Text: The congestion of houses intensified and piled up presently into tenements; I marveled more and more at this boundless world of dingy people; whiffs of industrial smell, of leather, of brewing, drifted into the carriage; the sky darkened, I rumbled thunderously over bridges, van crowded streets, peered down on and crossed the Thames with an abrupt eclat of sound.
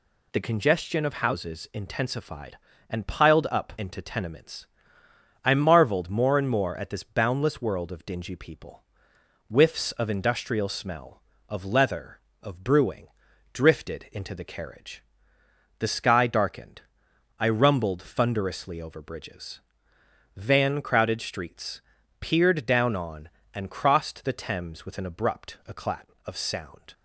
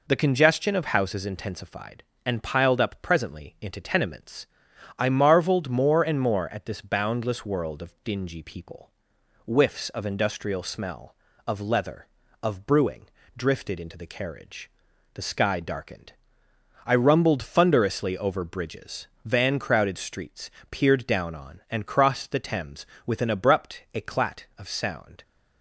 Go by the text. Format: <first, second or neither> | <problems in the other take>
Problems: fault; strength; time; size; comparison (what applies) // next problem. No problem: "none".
second | skips "presently"; at 3.7 s